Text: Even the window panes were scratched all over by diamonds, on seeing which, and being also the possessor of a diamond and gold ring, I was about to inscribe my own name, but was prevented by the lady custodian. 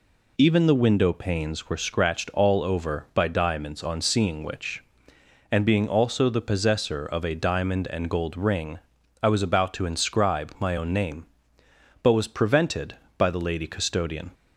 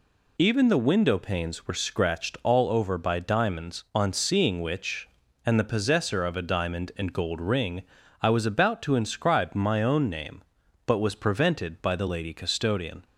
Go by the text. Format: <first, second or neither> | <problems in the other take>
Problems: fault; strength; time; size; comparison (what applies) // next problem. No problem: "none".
first | skips "being also"; at 5.6 s